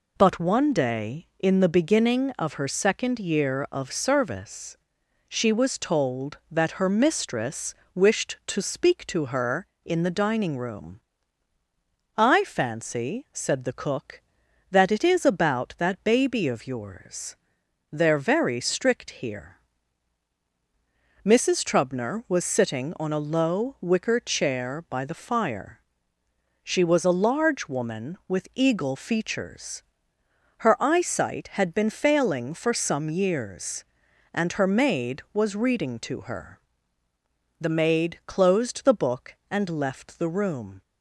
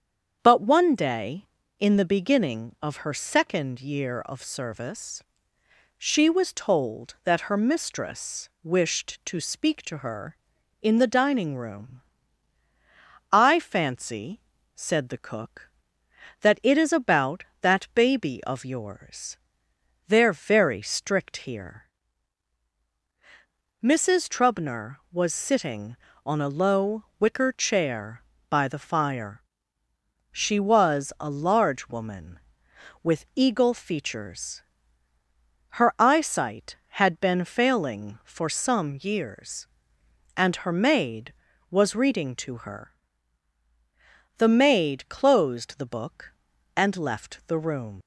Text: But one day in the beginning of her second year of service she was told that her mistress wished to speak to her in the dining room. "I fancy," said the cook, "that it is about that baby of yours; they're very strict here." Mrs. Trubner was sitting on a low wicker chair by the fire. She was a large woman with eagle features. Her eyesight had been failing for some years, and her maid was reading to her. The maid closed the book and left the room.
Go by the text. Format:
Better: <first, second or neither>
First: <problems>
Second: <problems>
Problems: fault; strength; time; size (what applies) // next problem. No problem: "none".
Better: first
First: pauses between "service" and "she"; noticeable; at 4.7 s; 0.50 s long // pauses between "mistress" and "wished"; slight; at 7.7 s; 0.20 s long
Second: starts louder than the rest; strong; until 1.4 s; 8 dB // pauses between "service" and "she"; noticeable; at 5.2 s; 0.80 s long // pauses between "mistress" and "wished"; slight; at 8.4 s; 0.16 s long // pauses between "low" and "wicker"; slight; at 27.0 s; 0.16 s long // leaves "room" unfinished; at 48.0 s; 95 ms